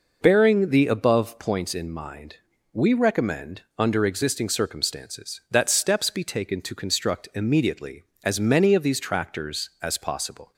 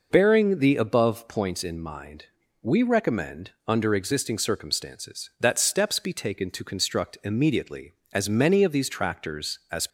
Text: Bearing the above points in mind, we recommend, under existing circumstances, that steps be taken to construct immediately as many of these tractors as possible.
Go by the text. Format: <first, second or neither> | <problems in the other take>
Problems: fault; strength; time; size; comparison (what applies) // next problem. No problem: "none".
first | stops before "possible"; at 9.8 s